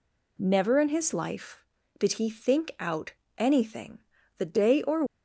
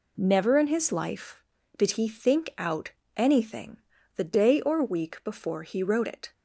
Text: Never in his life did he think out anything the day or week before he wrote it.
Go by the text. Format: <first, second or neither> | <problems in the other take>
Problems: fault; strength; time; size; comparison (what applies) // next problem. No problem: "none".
second | pauses between "out" and "anything"; slight; at 3.1 s; 0.26 s long; slight in the second // pauses between "anything" and "the"; at 3.9 s; 0.40 s long; also in the second // stops before "week before he wrote it"; at 5.0 s